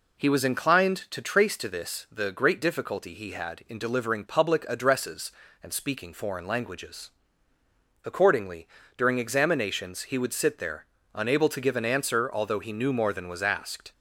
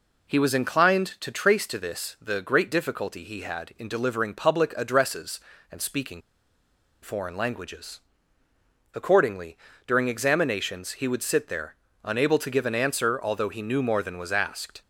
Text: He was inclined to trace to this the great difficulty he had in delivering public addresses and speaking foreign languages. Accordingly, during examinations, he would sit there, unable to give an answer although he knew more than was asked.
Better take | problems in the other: first | pauses between "speaking" and "foreign"; noticeable; at 6.2 s; 0.81 s long

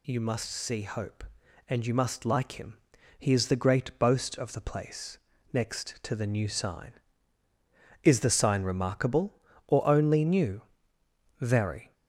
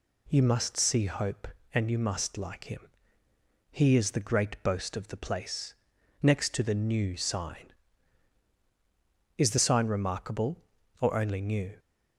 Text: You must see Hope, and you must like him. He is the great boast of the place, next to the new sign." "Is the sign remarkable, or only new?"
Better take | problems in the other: second | goes on to say "Very"; from 11.3 s on; 0.54 s long

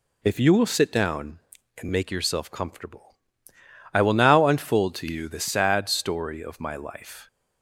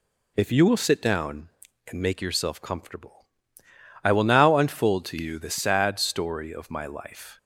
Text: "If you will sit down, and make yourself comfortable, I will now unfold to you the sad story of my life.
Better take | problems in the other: neither | none

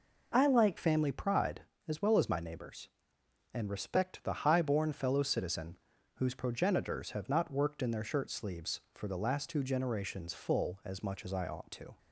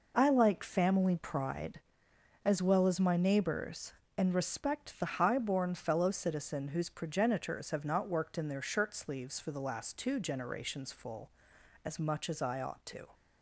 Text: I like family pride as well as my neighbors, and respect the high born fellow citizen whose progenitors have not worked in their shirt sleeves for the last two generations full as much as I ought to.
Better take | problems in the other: second | changes voice at "family"; from 0.7 s on; 11.2 s long // pauses between "citizen" and "whose"; at 5.7 s; 0.38 s long

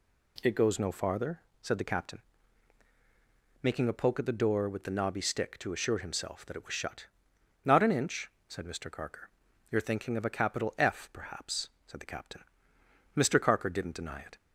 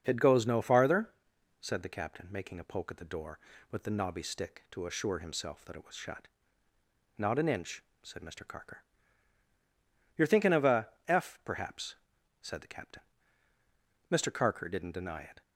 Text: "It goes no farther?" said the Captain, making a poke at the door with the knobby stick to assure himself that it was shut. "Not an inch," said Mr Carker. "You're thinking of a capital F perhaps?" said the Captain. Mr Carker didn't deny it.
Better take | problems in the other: first | starts louder than the rest; until 1.0 s; 6.5 dB // skips "capital"; at 10.9 s

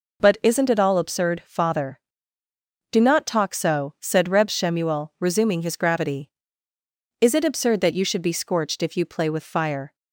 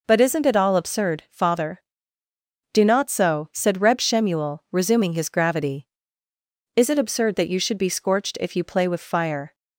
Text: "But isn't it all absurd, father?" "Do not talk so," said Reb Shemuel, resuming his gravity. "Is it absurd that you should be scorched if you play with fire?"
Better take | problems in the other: first | skips "talk"; at 3.0 s

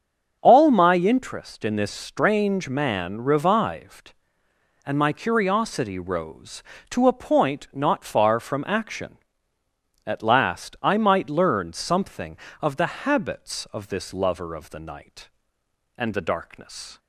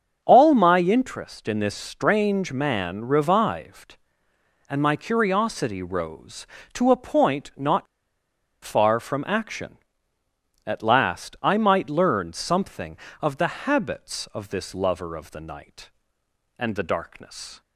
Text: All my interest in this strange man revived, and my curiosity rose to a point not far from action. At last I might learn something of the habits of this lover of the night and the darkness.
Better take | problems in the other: first | starts louder than the rest; until 1.2 s; 6.5 dB; also in the first // pauses between "not" and "far"; noticeable; at 7.8 s; 0.78 s long

